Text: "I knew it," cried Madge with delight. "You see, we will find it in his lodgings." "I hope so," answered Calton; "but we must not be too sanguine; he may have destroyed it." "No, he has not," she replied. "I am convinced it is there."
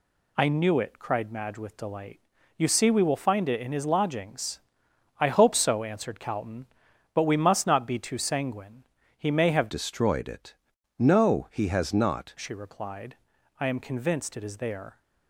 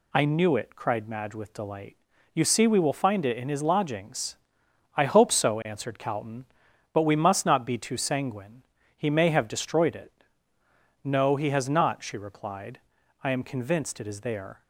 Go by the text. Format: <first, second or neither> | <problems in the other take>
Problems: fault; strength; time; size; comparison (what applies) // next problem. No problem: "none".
second | changes voice from "destroyed" to "not"; from 9.6 to 12.3 s; 2.7 s long